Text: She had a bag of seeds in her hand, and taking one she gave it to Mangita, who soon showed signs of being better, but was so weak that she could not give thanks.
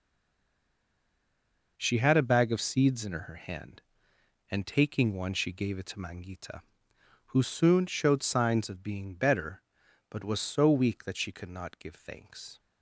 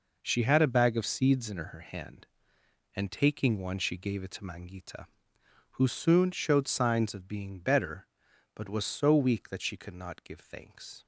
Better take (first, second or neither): second